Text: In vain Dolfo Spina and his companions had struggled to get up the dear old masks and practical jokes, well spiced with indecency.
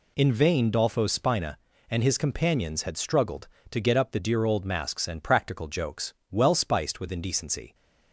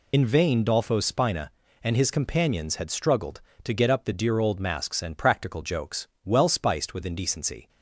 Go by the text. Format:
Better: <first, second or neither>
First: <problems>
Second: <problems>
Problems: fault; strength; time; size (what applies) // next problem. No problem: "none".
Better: first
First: none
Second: loses the start of "In"; at 0.1 s; 40 ms